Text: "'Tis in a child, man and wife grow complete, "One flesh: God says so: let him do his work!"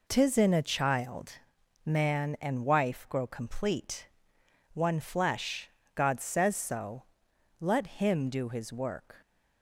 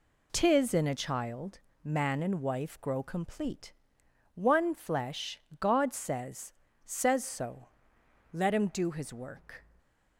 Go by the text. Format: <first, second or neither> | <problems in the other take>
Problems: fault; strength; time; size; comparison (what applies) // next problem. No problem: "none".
first | says "says" twice; at 6.8 s